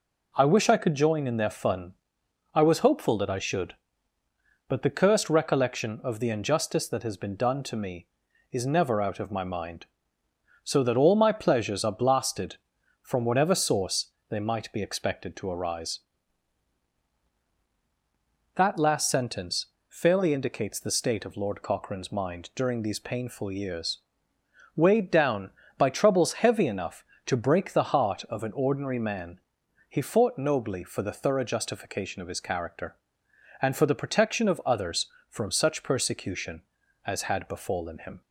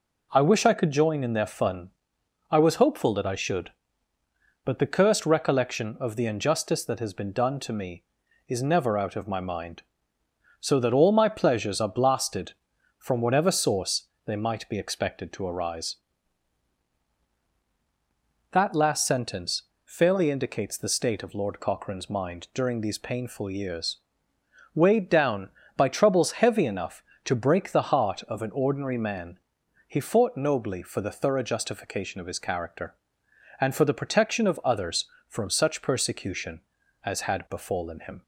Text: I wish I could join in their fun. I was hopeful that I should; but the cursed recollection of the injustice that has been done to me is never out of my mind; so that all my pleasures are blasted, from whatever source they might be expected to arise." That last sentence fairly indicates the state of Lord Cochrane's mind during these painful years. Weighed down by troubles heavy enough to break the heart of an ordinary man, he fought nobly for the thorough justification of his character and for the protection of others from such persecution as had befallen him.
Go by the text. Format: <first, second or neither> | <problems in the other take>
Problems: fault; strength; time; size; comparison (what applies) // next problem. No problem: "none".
neither | pauses between "source" and "they"; slight; the same in both // pauses between "sentence" and "fairly"; slight; the same in both